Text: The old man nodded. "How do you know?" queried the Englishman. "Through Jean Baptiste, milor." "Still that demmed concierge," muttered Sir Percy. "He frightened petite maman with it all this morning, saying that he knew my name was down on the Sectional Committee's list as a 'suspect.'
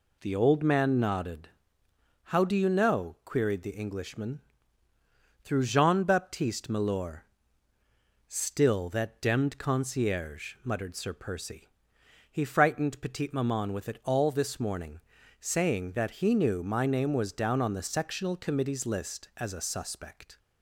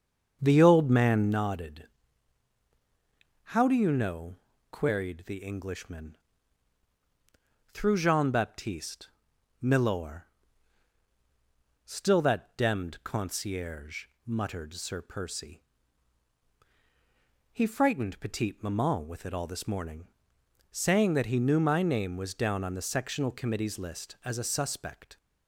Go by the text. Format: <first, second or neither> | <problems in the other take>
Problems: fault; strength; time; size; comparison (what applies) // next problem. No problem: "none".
first | starts louder than the rest; until 1.6 s; 7 dB